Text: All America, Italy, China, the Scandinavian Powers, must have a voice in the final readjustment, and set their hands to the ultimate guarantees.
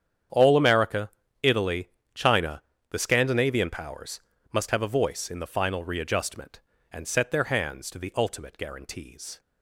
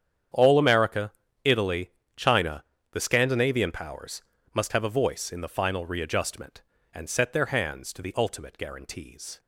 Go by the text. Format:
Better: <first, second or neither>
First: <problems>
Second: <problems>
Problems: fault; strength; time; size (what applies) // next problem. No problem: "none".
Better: neither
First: starts louder than the rest; strong; until 1.6 s; 8.5 dB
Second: starts louder than the rest; strong; until 1.6 s; 8.5 dB